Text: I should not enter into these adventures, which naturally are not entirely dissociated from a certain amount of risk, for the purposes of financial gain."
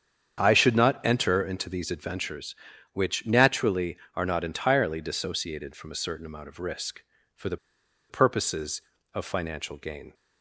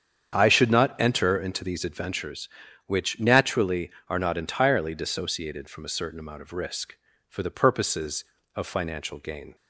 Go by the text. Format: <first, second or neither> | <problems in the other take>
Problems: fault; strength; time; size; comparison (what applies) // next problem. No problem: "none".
second | starts louder than the rest; strong; until 1.4 s; 8 dB; strong in the second // pauses between "the" and "purposes"; noticeable; at 7.5 s; 0.52 s long